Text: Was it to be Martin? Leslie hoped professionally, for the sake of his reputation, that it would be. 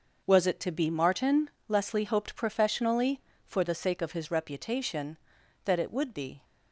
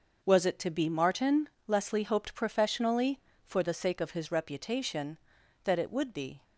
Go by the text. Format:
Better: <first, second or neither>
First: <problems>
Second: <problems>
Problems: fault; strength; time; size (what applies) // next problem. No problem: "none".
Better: neither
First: none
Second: none